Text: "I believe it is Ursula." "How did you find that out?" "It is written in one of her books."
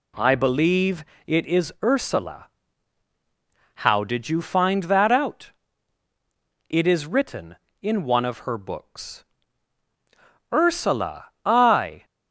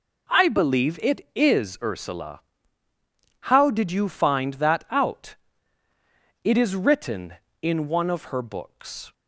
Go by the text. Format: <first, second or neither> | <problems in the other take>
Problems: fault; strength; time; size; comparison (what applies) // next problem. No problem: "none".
second | pauses between "believe" and "it"; slight; at 1.0 s; 0.24 s long // goes on to say "Ursula I"; from 10.5 s on; 1.5 s long